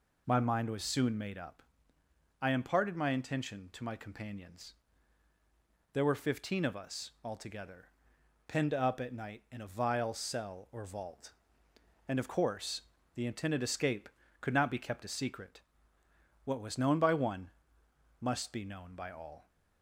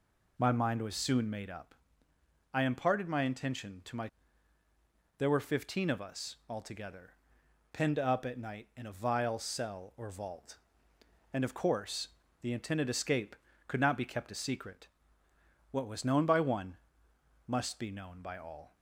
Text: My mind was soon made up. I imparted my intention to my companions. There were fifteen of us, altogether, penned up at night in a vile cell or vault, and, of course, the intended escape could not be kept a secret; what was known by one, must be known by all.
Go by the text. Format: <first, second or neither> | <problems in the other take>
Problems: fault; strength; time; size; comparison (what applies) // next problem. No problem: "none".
first | skips "companions"; at 4.6 s